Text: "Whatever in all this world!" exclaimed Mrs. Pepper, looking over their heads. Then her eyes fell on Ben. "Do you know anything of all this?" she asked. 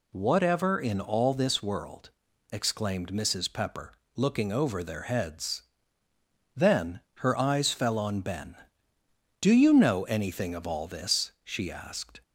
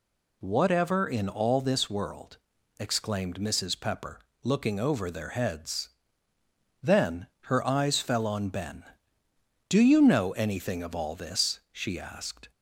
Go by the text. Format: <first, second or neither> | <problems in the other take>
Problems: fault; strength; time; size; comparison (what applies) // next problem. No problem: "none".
neither | pauses between "Then" and "her"; slight; the same in both